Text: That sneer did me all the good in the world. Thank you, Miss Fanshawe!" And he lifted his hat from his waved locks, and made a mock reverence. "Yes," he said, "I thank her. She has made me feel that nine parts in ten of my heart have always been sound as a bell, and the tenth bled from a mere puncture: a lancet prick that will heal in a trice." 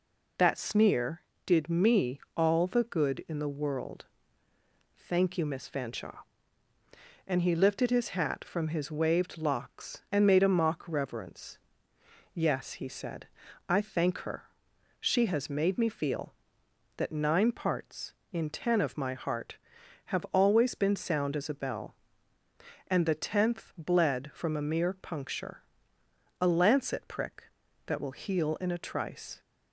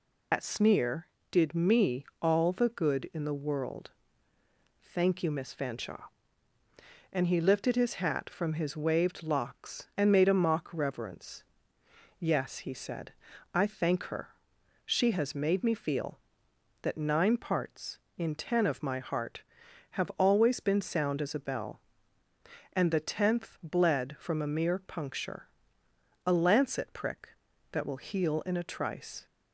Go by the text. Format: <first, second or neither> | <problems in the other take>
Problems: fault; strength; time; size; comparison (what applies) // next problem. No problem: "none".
first | loses the start of "That"; at 0.3 s; 85 ms // pauses between "me" and "all"; slight; at 2.0 s; 0.18 s long; slight in the first